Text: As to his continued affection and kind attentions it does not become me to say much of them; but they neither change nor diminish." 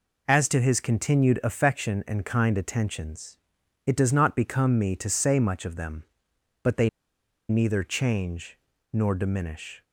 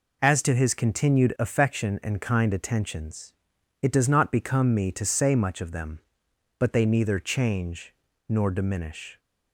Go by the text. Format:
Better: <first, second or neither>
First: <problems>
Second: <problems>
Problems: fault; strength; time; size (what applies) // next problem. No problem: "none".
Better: second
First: pauses between "attentions" and "it"; noticeable; at 3.3 s; 0.48 s long // pauses between "they" and "neither"; noticeable; at 6.8 s; 0.60 s long // pauses between "change" and "nor"; slight; at 8.5 s; 0.34 s long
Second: pauses between "attentions" and "it"; noticeable; at 3.3 s; 0.48 s long // pauses between "change" and "nor"; slight; at 7.9 s; 0.34 s long